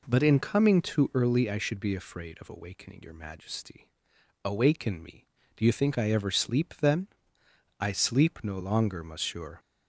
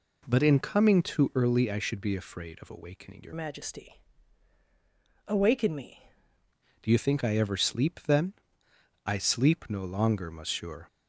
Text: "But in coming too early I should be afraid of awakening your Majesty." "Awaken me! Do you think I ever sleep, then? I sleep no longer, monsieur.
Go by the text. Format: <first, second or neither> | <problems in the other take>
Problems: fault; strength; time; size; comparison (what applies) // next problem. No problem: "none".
first | changes voice from "Majesty" to "me"; from 3.3 to 6.0 s; 2.7 s long